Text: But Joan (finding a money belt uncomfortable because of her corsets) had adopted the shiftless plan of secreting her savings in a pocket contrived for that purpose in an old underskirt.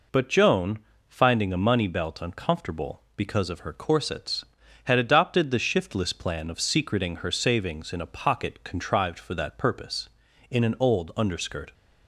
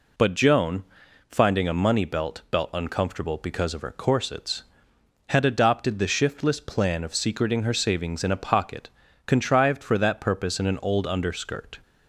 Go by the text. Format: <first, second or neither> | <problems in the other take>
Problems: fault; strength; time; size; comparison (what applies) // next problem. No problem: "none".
first | says "belt" twice; at 2.4 s // pauses between "pocket" and "contrived"; at 8.8 s; 0.38 s long